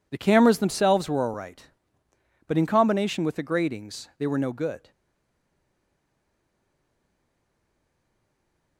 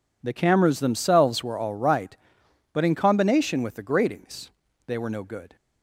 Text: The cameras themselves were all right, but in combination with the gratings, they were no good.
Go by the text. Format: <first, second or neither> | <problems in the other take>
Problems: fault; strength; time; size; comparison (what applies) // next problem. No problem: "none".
second | stays silent after the last word; strong; from 4.9 s on; 3.8 s long